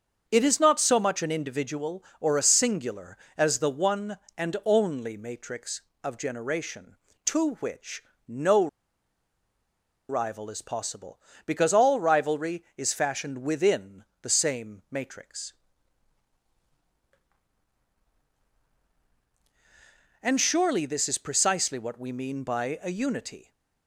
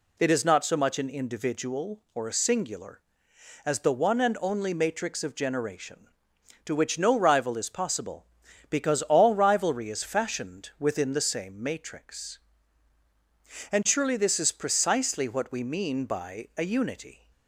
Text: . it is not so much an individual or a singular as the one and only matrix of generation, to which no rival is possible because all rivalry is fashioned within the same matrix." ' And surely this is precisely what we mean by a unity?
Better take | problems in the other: second | starts louder than the rest; until 1.2 s; 7 dB // pauses between "which" and "no"; slight; at 8.0 s; 0.24 s long // pauses between "no" and "rival"; strong; at 8.6 s; 1.4 s long // pauses between "within" and "the"; slight; at 14.0 s; 0.16 s long

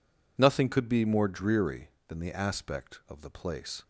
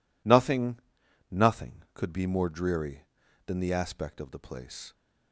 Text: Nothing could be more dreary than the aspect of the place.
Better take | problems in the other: first | says "Nothing" twice; at 1.3 s

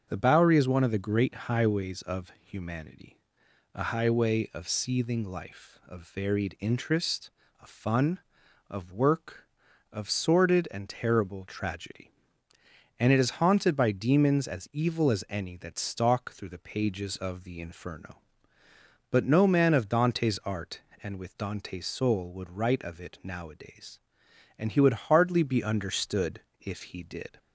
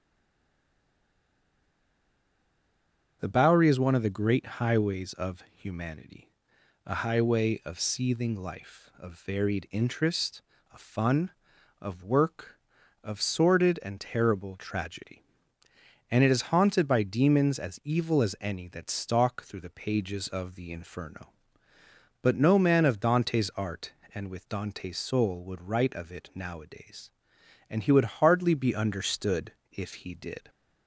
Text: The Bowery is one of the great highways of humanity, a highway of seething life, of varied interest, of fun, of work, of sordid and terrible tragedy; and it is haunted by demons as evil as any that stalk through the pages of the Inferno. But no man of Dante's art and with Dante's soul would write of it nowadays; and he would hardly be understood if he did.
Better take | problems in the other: first | stays silent before the first word; strong; until 3.2 s; 3.2 s long // starts louder than the rest; until 4.2 s; 6.5 dB; also in the first // pauses between "understood" and "if"; slight; at 29.5 s; 0.18 s long; slight in the first

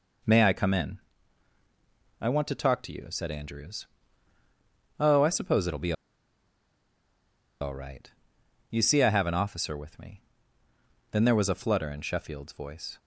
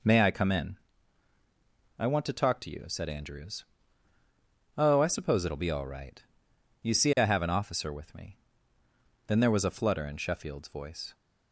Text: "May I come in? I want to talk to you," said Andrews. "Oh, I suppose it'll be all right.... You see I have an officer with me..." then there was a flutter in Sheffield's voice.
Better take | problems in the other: second | pauses between "be" and "all"; strong; at 5.9 s; 1.6 s long

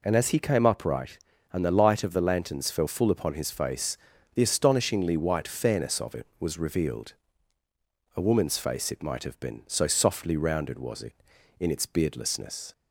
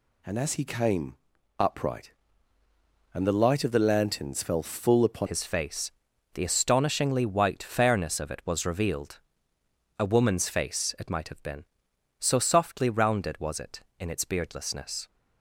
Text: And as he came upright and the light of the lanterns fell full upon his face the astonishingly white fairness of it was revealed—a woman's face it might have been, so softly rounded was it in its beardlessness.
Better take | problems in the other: first | pauses between "came" and "upright"; at 1.1 s; 0.42 s long // changes voice at "his"; from 5.2 s on; 9.8 s long // pauses between "face" and "the"; at 5.9 s; 0.42 s long; also in the first

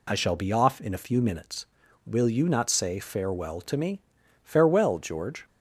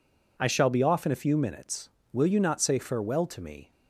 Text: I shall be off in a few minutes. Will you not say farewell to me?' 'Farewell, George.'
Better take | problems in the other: first | stops before "Farewell George"; at 3.7 s

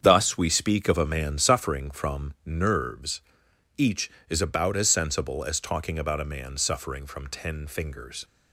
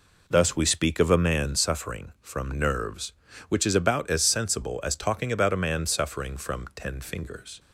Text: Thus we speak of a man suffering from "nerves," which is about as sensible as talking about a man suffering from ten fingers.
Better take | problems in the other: second | starts louder than the rest; strong; until 1.0 s; 7.5 dB // says "each" for "which"; at 3.7 s

